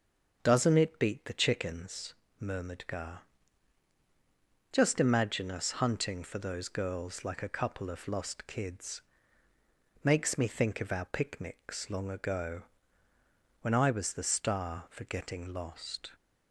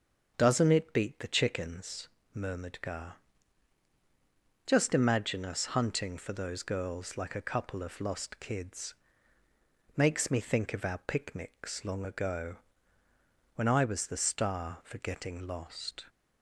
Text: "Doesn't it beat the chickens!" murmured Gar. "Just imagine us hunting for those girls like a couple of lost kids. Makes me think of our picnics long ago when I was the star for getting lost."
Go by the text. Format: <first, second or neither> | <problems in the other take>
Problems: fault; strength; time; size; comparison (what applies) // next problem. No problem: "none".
neither | starts louder than the rest; the same in both // pauses between "ago" and "when"; the same in both